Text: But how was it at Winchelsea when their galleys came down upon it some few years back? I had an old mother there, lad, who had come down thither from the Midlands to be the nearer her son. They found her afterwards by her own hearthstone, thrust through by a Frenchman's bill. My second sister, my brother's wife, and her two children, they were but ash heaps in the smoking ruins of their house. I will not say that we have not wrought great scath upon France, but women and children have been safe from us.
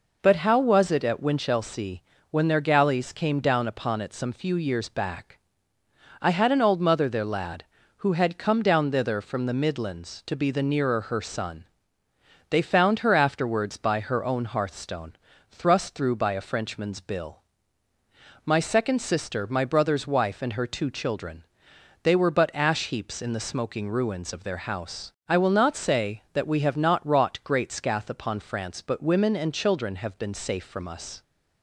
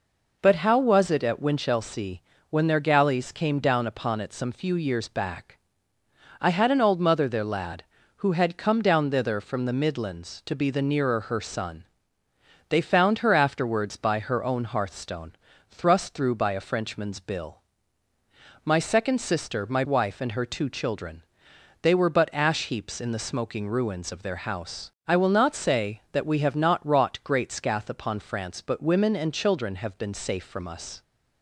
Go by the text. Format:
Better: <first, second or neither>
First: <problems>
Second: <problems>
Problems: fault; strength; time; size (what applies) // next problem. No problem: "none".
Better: first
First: pauses between "Winchelsea" and "when"; slight; at 2.0 s; 0.28 s long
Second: pauses between "Winchelsea" and "when"; slight; at 2.2 s; 0.28 s long // skips "brother's"; at 19.8 s